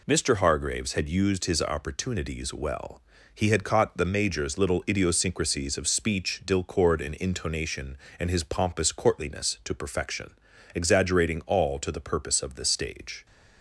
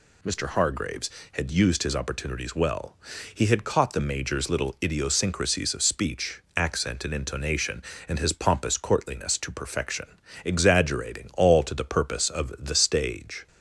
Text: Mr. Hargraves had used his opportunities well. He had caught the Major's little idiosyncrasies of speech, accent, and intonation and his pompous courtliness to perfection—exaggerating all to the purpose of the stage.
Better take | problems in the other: second | says "dilcord" for "accent"; at 6.4 s

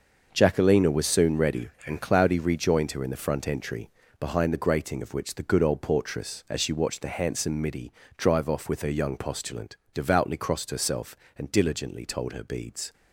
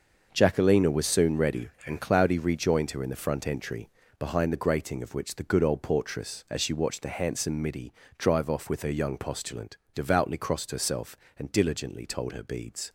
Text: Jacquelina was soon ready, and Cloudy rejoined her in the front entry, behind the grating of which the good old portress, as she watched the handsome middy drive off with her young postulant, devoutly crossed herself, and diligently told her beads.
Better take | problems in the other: neither | starts louder than the rest; the same in both // pauses between "middy" and "drive"; slight; the same in both

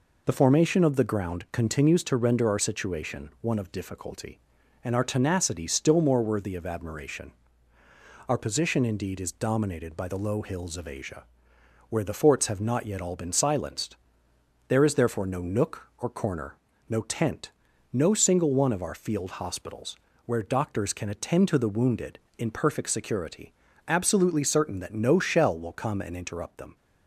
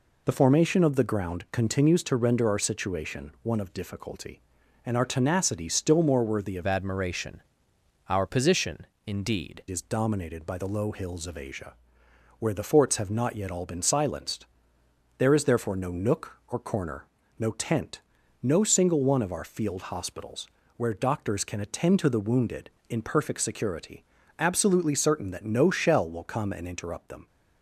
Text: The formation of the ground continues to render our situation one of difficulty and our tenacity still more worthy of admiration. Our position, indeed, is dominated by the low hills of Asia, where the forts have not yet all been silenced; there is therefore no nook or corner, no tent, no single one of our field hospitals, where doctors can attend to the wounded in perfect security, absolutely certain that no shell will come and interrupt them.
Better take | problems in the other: first | changes voice from "admiration" to "indeed"; from 6.6 to 9.6 s; 3.0 s long

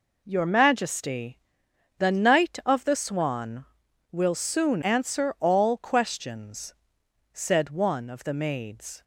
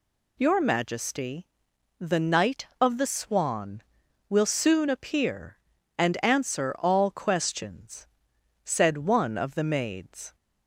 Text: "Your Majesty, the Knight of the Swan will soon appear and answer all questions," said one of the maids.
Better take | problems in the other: second | skips "appear and"; at 4.8 s

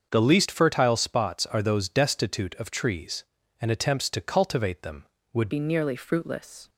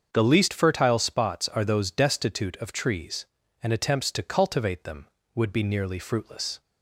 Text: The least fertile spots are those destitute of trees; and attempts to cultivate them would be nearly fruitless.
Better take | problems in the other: second | starts louder than the rest; until 1.1 s; 6.5 dB; also in the second // changes voice at "be"; from 5.4 s on; 1.2 s long

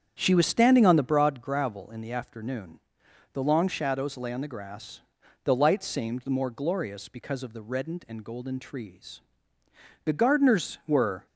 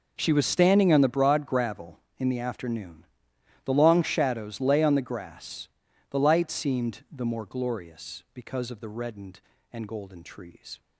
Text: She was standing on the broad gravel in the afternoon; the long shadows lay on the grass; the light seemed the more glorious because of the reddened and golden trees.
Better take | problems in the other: second | starts louder than the rest; strong; until 1.2 s; 8.5 dB // goes on to say "The gardeners were"; noticeable; from 10.0 s on; 1.2 s long

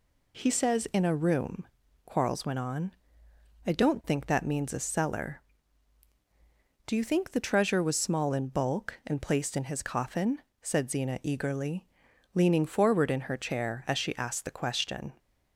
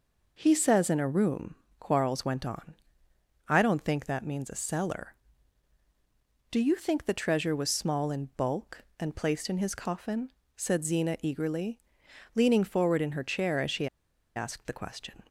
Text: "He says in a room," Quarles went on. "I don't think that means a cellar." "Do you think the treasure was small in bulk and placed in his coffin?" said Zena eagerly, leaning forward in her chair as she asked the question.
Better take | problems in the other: first | pauses between "she" and "asked"; noticeable; at 13.8 s; 0.48 s long

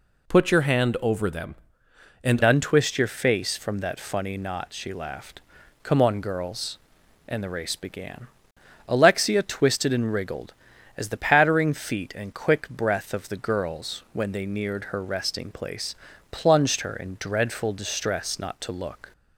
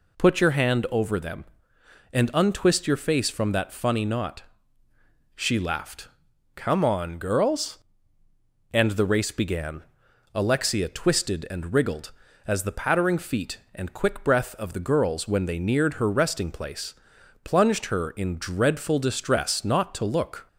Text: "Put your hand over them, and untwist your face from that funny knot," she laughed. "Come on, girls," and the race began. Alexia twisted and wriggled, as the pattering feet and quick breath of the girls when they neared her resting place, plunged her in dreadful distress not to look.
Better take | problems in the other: second | changes voice at "untwist"; from 2.4 s on; 16.7 s long

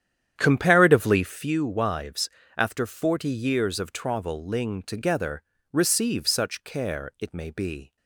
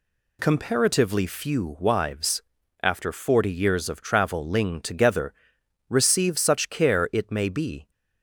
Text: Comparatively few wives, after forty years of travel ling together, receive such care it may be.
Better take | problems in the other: second | starts louder than the rest; strong; until 1.6 s; 9.5 dB

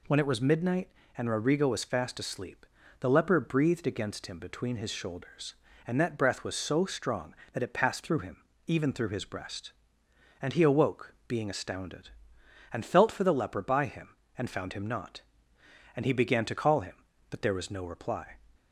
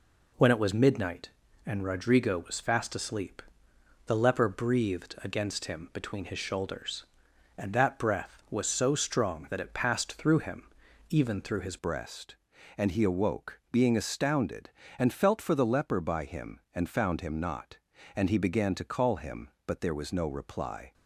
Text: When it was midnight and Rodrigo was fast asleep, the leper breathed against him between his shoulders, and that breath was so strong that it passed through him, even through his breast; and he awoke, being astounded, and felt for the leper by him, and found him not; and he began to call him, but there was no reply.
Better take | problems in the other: first | changes voice at "breast"; from 11.7 s on; 9.2 s long

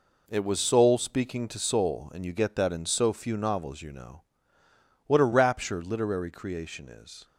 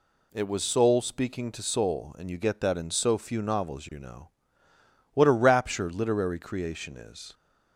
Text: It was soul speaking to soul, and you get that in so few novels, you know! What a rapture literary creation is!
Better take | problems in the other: second | gets quieter; strong; throughout; 8.5 dB

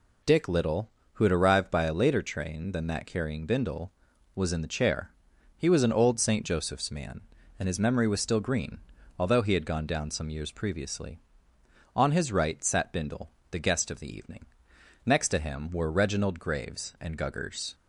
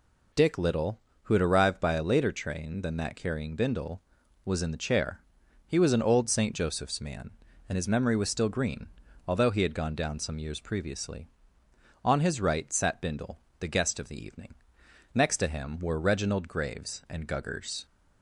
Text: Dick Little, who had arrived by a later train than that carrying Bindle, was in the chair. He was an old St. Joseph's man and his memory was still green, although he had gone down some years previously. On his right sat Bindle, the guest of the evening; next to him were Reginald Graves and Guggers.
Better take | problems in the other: neither | none

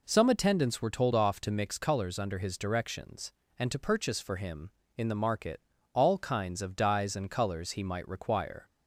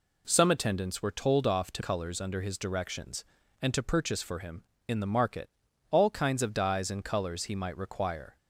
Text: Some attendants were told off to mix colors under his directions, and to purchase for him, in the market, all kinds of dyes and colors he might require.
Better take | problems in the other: first | skips "mix"; at 1.8 s

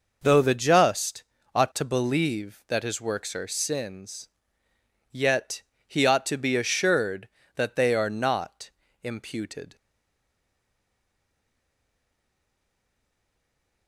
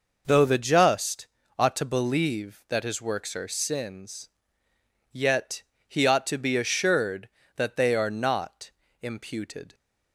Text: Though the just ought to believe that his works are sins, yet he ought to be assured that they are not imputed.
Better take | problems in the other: second | pauses between "just" and "ought"; slight; at 1.2 s; 0.30 s long; slight in the second // pauses between "yet" and "he"; slight; at 5.6 s; 0.26 s long; slight in the second // pauses between "not" and "imputed"; slight; at 8.7 s; 0.32 s long; slight in the second // stays silent after the last word; strong; from 9.7 s on; 4.1 s long

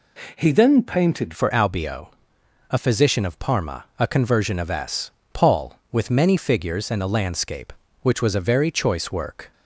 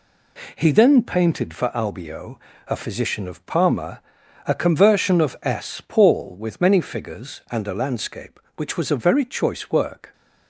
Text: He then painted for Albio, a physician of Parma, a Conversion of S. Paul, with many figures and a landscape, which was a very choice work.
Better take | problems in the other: second | changes voice at "for"; from 1.3 s on; 8.2 s long

